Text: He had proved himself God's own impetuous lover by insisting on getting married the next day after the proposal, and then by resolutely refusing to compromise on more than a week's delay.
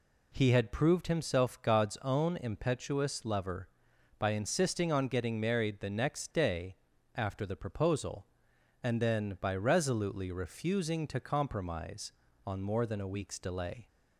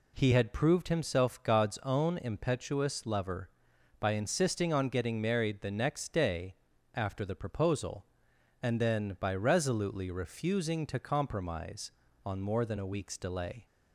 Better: neither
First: pauses between "day" and "after"; at 6.7 s; 0.40 s long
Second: pauses between "day" and "after"; at 6.5 s; 0.40 s long

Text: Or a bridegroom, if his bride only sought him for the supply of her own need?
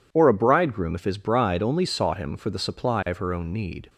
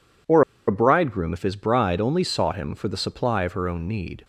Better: first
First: none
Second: pauses between "Or" and "a"; slight; at 0.4 s; 0.27 s long

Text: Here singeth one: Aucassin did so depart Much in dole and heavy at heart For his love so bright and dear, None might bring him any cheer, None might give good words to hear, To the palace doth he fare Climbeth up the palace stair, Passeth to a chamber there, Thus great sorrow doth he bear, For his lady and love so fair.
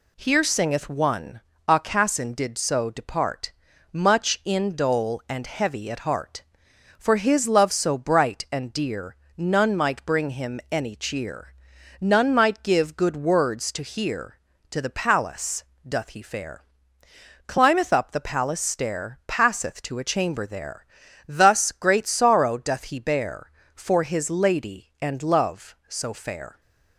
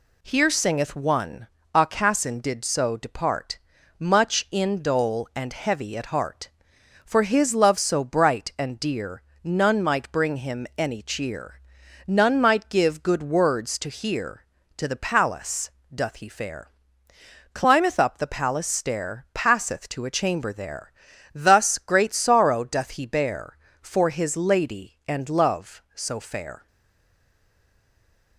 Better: first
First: pauses between "depart" and "Much"; at 3.5 s; 0.42 s long // pauses between "palace" and "doth"; slight; at 15.6 s; 0.22 s long // pauses between "fare" and "Climbeth"; noticeable; at 16.6 s; 0.86 s long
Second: pauses between "depart" and "Much"; at 3.5 s; 0.42 s long // pauses between "palace" and "doth"; slight; at 15.7 s; 0.22 s long // pauses between "fare" and "Climbeth"; noticeable; at 16.6 s; 0.86 s long // stays silent after the last word; noticeable; from 26.6 s on; 1.7 s long

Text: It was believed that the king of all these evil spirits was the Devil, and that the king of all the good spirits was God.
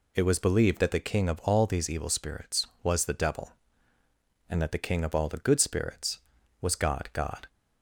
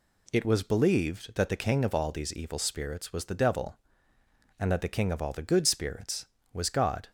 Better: second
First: says "God" twice; at 7.1 s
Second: none

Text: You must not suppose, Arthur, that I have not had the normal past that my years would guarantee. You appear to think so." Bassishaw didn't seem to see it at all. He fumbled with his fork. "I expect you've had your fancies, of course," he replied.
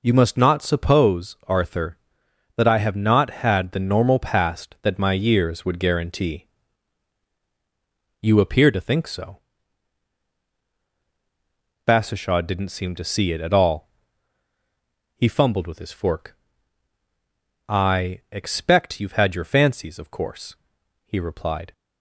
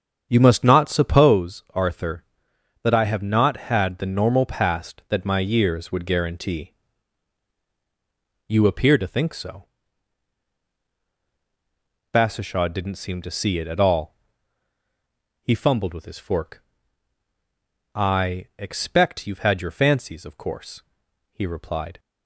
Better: first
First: none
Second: starts louder than the rest; strong; until 1.4 s; 8 dB

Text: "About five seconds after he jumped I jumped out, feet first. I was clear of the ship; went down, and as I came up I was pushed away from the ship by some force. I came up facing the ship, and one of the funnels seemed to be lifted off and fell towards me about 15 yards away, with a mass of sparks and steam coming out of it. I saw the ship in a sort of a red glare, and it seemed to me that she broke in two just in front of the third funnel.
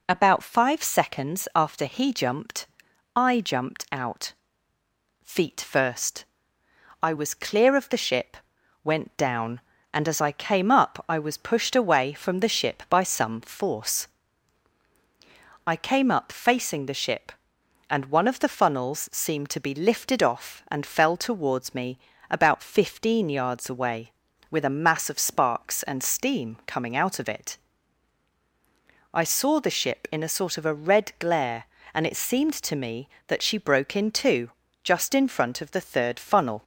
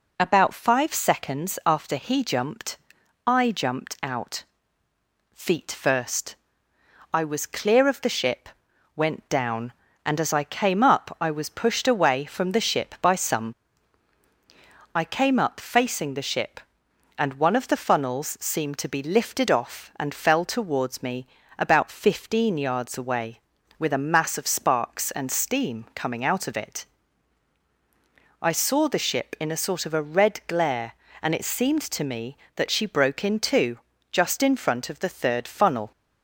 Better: first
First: pauses between "jumped" and "I"; noticeable; at 2.6 s; 0.50 s long // pauses between "me" and "about"; slight; at 21.9 s; 0.32 s long // pauses between "two" and "just"; slight; at 34.4 s; 0.34 s long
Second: pauses between "jumped" and "I"; noticeable; at 2.7 s; 0.50 s long // skips "force"; at 14.2 s // pauses between "me" and "about"; slight; at 21.2 s; 0.32 s long // pauses between "two" and "just"; slight; at 33.7 s; 0.34 s long

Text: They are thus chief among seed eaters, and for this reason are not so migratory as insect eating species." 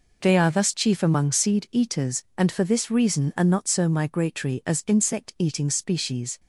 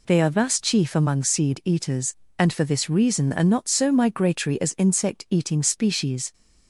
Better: neither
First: none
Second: none

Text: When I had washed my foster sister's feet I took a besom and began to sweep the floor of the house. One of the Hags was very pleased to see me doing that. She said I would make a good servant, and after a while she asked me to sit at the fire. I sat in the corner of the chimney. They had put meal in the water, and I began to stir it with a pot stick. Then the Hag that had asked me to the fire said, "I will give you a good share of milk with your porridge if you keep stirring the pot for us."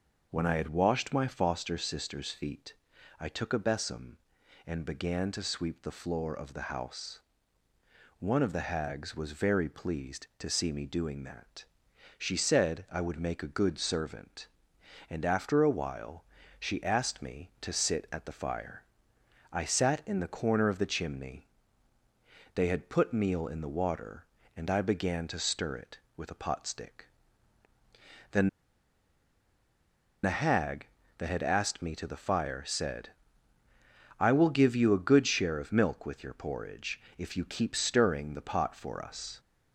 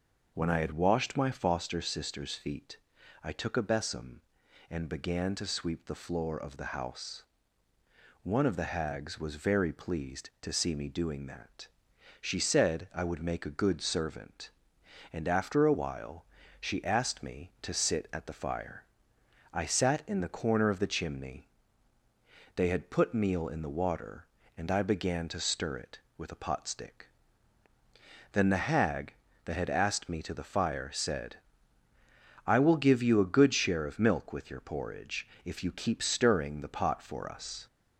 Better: second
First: starts louder than the rest; until 1.3 s; 6 dB // pauses between "feet" and "I"; noticeable; at 2.7 s; 0.46 s long // pauses between "while" and "she"; slight; at 16.2 s; 0.36 s long // pauses between "Then" and "the"; strong; at 28.4 s; 1.7 s long // pauses between "porridge" and "if"; slight; at 36.9 s; 0.18 s long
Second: starts louder than the rest; until 1.3 s; 6 dB // pauses between "feet" and "I"; noticeable; at 2.7 s; 0.46 s long // pauses between "while" and "she"; slight; at 16.2 s; 0.36 s long // pauses between "porridge" and "if"; slight; at 35.2 s; 0.18 s long

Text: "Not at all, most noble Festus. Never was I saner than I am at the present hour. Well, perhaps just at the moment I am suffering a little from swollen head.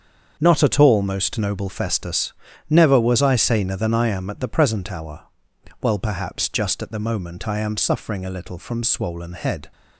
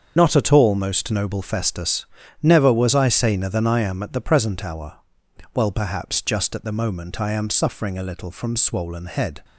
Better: first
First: starts louder than the rest; until 1.4 s; 6.5 dB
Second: loses the start of "Not"; at 0.1 s; 40 ms // starts louder than the rest; until 1.1 s; 6.5 dB

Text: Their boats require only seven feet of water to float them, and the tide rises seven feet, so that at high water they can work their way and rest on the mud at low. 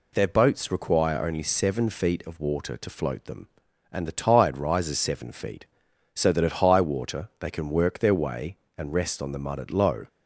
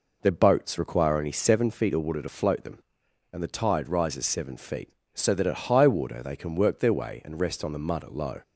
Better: first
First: none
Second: starts louder than the rest; noticeable; until 1.8 s; 4.5 dB

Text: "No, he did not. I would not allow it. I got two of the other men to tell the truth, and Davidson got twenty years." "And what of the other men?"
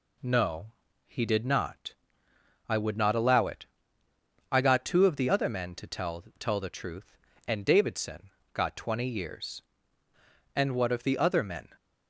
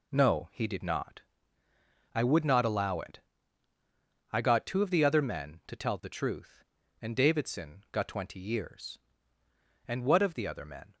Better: second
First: says "tell" twice; at 6.3 s // pauses between "Davidson" and "got"; slight; at 8.3 s; 0.24 s long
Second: none

